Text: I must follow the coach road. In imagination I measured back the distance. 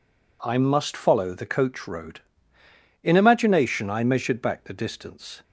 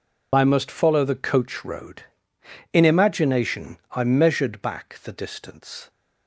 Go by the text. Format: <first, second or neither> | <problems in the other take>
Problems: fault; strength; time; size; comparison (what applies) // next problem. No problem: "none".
first | loses the start of "I"; at 0.3 s; 65 ms